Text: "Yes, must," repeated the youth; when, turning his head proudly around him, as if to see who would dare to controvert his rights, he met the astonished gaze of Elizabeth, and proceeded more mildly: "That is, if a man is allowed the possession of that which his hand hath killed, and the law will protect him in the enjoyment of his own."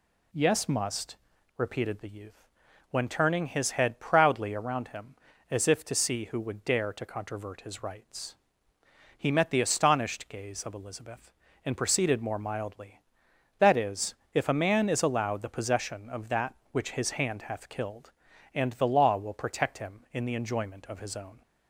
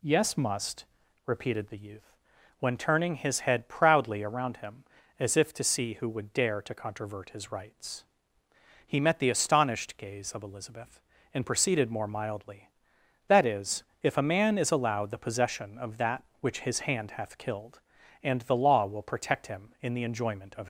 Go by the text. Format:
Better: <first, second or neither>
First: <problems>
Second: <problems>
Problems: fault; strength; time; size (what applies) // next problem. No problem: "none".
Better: first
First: none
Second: stops before "his own"; at 20.6 s